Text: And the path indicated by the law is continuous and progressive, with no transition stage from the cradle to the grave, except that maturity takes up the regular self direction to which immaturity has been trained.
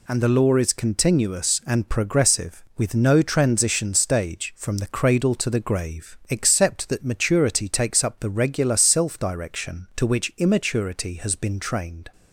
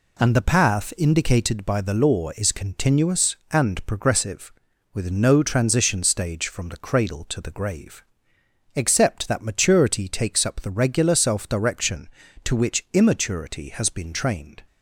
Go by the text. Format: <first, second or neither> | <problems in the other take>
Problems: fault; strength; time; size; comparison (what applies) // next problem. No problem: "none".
second | skips "the path indicated by"; at 0.2 s